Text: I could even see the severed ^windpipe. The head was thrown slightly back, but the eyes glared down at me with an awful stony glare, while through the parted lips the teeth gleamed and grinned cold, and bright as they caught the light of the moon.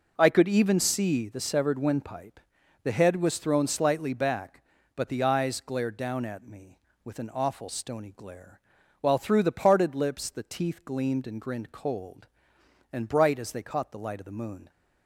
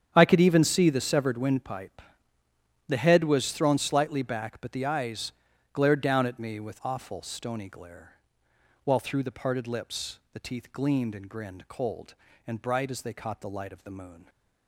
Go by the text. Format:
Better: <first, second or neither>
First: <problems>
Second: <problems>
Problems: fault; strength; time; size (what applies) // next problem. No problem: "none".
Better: first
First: none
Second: starts louder than the rest; strong; until 1.1 s; 9 dB // pauses between "eyes" and "glared"; at 5.3 s; 0.42 s long // skips "an"; at 6.8 s